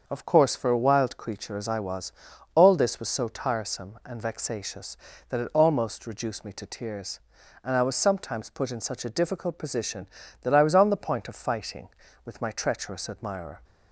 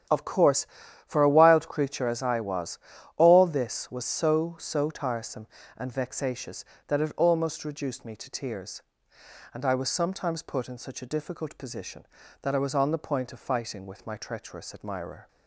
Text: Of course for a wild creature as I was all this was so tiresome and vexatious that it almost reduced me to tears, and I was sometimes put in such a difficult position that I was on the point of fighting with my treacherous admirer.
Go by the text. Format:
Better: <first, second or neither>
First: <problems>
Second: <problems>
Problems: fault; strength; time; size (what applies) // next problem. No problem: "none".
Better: first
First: starts louder than the rest; until 1.0 s; 6.5 dB // pauses between "was" and "all"; at 2.1 s; 0.42 s long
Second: starts louder than the rest; strong; until 1.5 s; 9.5 dB // pauses between "was" and "all"; at 2.7 s; 0.40 s long // says "so" twice; at 4.5 s